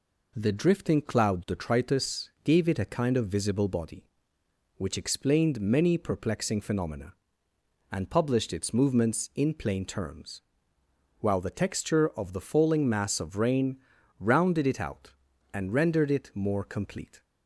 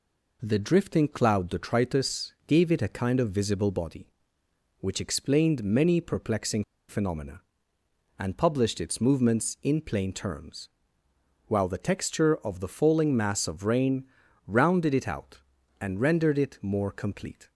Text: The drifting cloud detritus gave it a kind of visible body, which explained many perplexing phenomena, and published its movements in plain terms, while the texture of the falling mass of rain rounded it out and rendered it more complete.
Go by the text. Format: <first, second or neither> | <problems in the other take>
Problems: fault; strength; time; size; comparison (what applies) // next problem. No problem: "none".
first | pauses between "perplexing" and "phenomena"; slight; at 6.6 s; 0.25 s long // pauses between "rain" and "rounded"; at 14.0 s; 0.42 s long; also in the first